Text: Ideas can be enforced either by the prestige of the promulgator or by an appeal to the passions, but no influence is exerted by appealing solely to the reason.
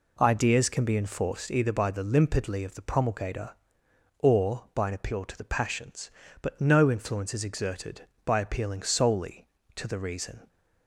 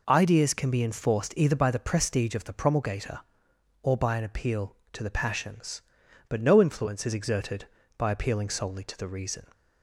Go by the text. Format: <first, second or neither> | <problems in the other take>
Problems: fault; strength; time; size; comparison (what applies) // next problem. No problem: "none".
second | says "limpidly" for "prestige"; at 2.0 s